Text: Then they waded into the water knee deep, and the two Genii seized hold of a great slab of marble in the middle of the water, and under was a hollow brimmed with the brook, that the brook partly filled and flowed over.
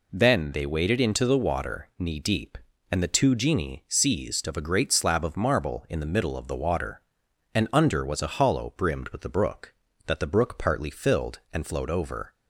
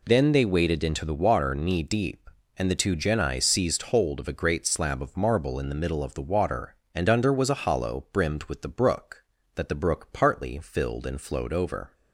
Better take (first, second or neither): second